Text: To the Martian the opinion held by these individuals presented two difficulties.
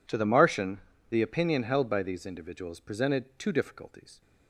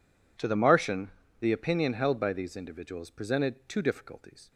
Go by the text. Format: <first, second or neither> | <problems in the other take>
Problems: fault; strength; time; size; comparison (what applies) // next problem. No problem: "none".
neither | pauses between "Martian" and "the"; slight; the same in both